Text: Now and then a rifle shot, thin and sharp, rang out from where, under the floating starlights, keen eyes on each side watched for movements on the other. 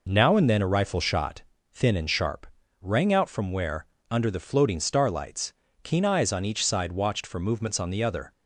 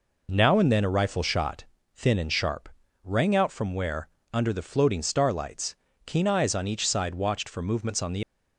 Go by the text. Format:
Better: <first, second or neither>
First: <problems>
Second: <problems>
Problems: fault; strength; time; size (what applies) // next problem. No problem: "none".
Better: first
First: none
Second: stops before "other"; at 8.2 s